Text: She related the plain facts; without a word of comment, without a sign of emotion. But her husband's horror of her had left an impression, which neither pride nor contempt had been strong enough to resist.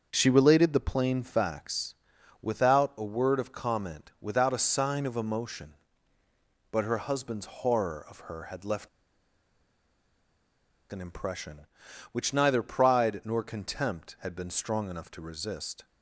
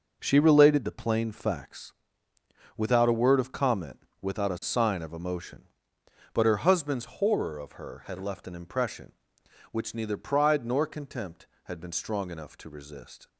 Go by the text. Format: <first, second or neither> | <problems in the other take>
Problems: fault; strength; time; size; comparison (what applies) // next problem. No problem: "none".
second | starts louder than the rest; until 1.1 s; 6.5 dB // pauses between "left" and "an"; strong; at 8.8 s; 2.0 s long